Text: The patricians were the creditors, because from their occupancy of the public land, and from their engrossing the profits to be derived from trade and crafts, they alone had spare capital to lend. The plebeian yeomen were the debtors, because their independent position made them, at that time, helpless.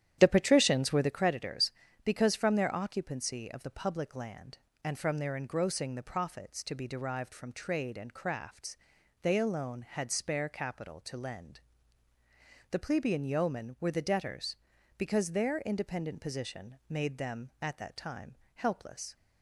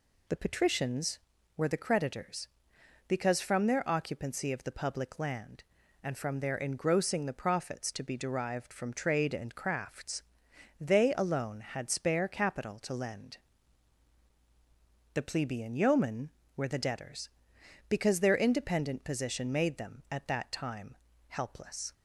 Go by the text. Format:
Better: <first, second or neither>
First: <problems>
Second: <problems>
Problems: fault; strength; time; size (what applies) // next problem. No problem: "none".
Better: second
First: starts louder than the rest; strong; until 1.2 s; 11 dB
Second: none